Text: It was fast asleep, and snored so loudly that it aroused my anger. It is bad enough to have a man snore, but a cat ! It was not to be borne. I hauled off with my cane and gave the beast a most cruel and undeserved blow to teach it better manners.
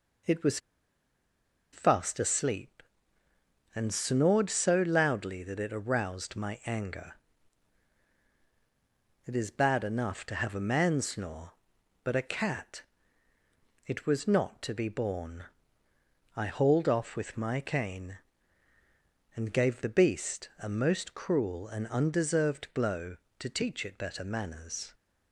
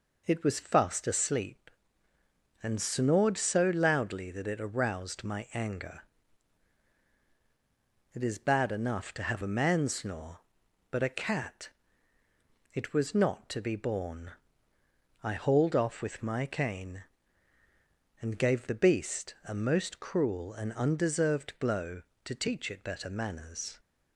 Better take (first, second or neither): second